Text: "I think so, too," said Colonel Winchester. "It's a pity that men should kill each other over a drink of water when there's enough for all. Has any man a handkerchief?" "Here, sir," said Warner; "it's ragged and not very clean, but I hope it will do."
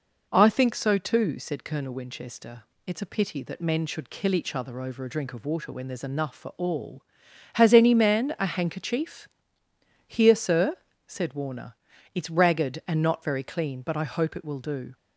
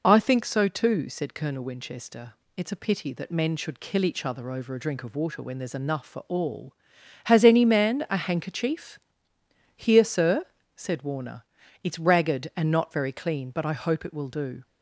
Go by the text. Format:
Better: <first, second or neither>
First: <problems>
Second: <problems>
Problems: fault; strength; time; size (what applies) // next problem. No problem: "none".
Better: first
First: none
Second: loses the start of "I"; at 0.0 s; 50 ms